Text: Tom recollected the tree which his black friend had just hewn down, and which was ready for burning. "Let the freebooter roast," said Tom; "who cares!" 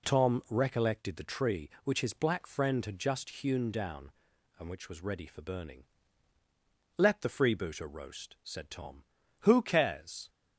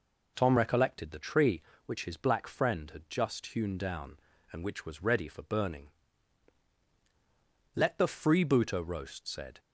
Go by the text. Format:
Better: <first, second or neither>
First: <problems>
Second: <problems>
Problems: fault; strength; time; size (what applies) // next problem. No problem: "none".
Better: first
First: none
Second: stops before "Tom who cares"; at 9.5 s